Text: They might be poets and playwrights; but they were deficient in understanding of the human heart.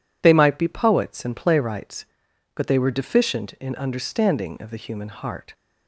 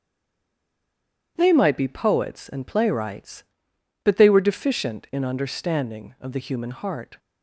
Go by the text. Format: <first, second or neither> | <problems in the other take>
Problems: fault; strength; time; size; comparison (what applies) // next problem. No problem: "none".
first | stays silent before the first word; noticeable; until 1.3 s; 1.3 s long // starts louder than the rest; strong; until 2.3 s; 9.5 dB